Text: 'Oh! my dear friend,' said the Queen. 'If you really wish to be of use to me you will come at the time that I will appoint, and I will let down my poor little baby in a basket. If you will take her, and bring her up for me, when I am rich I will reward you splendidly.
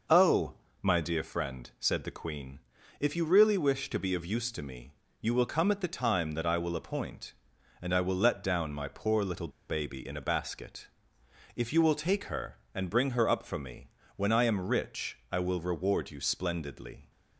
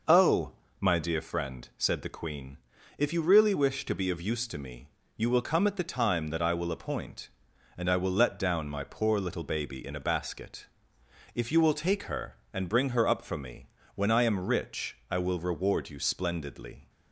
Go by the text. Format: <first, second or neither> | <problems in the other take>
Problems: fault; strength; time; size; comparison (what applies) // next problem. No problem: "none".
second | pauses between "me" and "you"; slight; at 4.9 s; 0.26 s long; slight in the second // pauses between "little" and "baby"; slight; at 9.4 s; 0.19 s long